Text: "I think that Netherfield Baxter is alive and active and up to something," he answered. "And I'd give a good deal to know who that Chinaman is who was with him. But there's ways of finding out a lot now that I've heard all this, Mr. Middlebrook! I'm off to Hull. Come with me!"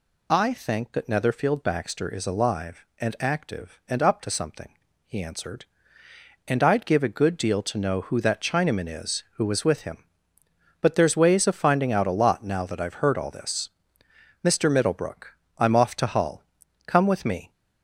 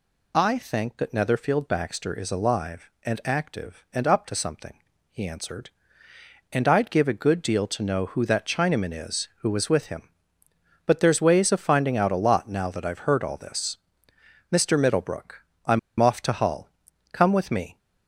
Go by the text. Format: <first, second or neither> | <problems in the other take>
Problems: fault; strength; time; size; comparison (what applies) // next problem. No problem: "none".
first | pauses between "I'm" and "off"; slight; at 15.7 s; 0.21 s long